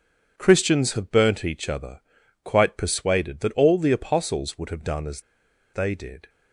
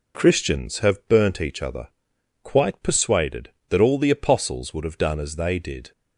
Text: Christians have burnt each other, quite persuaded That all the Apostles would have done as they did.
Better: second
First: pauses between "as" and "they"; noticeable; at 5.2 s; 0.51 s long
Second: none

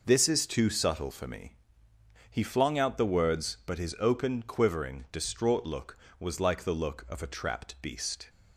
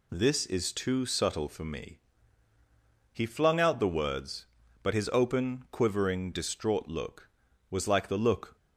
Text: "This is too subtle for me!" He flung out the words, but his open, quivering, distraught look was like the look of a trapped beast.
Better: first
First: none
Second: stops before "of a trapped beast"; at 8.5 s

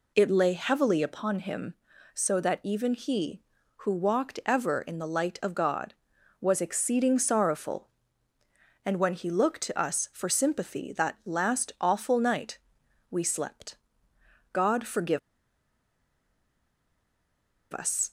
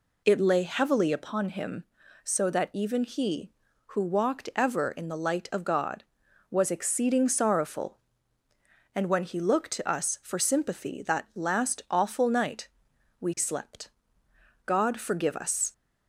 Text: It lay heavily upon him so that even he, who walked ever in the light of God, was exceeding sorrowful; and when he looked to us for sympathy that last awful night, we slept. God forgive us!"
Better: second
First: pauses between "forgive" and "us"; strong; at 15.1 s; 2.5 s long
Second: none

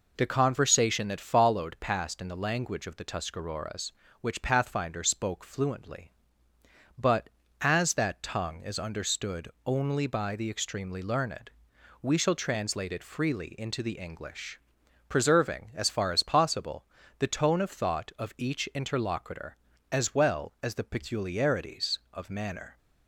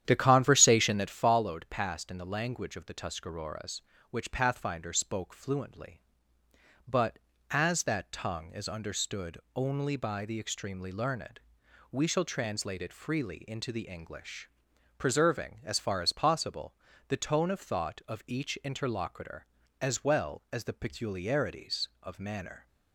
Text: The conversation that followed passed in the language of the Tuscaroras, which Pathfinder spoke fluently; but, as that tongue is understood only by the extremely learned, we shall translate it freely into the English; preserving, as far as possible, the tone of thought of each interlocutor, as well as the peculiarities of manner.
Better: first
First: pauses between "understood" and "only"; slight; at 9.4 s; 0.16 s long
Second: starts louder than the rest; strong; until 1.3 s; 10 dB // pauses between "understood" and "only"; slight; at 9.3 s; 0.16 s long

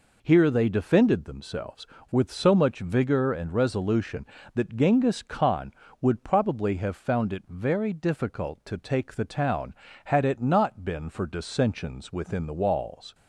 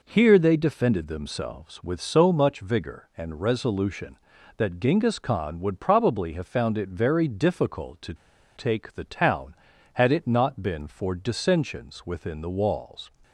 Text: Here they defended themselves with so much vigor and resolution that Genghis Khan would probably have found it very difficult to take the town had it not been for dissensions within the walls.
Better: first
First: none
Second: pauses between "to" and "take"; at 8.1 s; 0.42 s long

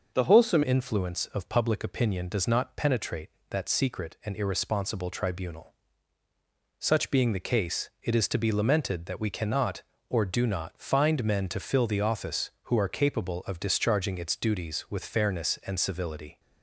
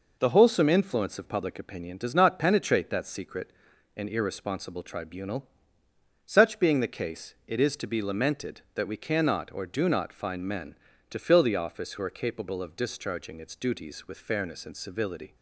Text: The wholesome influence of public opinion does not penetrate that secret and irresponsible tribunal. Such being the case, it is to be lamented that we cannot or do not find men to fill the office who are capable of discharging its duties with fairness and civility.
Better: second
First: changes voice at "influence"; from 0.6 s on; 15.7 s long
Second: none

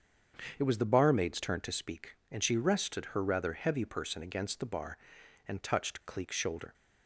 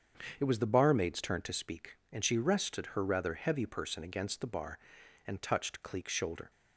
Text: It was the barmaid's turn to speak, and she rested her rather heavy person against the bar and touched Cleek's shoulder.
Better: neither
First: starts louder than the rest; strong; until 1.5 s; 7.5 dB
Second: starts louder than the rest; strong; until 1.4 s; 7.5 dB

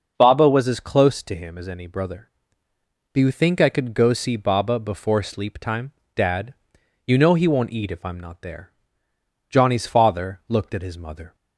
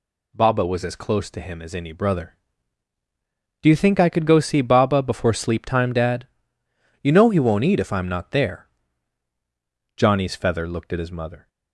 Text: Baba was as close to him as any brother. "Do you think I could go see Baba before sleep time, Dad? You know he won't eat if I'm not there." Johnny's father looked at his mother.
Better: first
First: none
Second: says "feather" for "father"; at 10.3 s

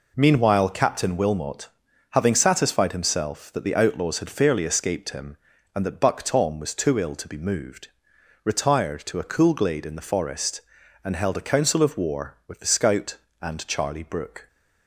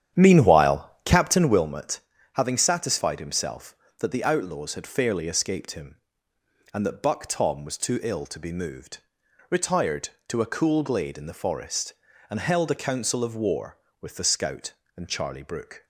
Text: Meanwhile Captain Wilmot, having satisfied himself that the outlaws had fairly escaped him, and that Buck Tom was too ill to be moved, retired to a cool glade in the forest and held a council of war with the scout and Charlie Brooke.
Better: first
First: none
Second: starts louder than the rest; strong; until 1.7 s; 9.5 dB // pauses between "Meanwhile" and "Captain"; slight; at 0.8 s; 0.16 s long

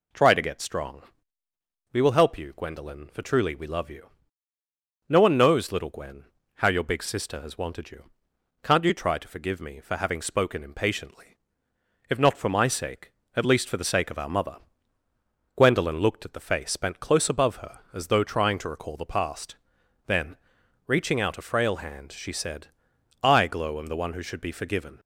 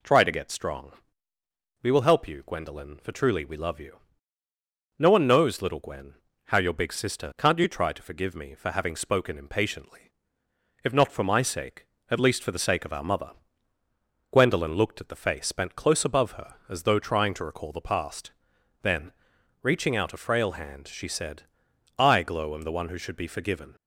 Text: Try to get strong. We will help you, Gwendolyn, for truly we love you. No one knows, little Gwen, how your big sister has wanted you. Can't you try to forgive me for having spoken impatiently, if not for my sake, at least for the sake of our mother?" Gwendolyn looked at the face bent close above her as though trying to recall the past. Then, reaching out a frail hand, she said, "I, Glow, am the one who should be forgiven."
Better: first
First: none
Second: skips "has wanted you"; at 7.3 s

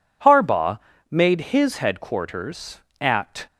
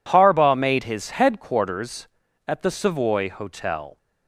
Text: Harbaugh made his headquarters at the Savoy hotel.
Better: second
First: pauses between "Harbaugh" and "made"; slight; at 0.8 s; 0.32 s long // stops before "the Savoy hotel"; at 3.4 s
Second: none

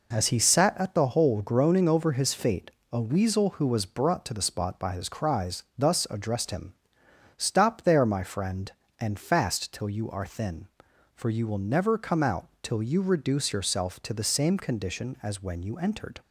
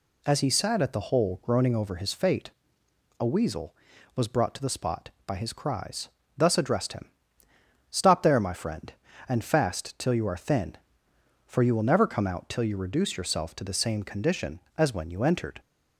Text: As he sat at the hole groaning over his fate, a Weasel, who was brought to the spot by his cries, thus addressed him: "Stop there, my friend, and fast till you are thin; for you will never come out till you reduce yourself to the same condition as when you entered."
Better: first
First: none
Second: skips "who"; at 3.9 s

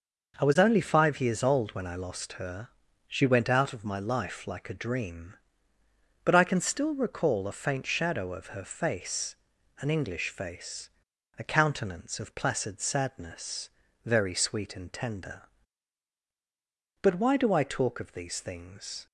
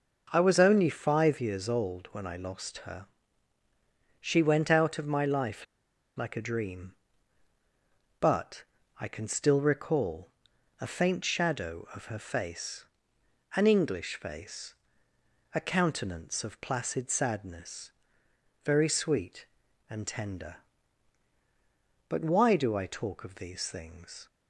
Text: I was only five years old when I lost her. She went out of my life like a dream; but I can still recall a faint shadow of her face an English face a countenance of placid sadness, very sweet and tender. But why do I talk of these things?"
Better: first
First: pauses between "face" and "an"; noticeable; at 9.3 s; 0.46 s long // pauses between "face" and "a"; noticeable; at 10.8 s; 0.48 s long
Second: pauses between "life" and "like"; noticeable; at 5.6 s; 0.52 s long // pauses between "but" and "I"; slight; at 8.6 s; 0.34 s long // pauses between "recall" and "a"; noticeable; at 10.2 s; 0.50 s long // pauses between "face" and "an"; noticeable; at 12.8 s; 0.70 s long // pauses between "face" and "a"; noticeable; at 14.7 s; 0.80 s long

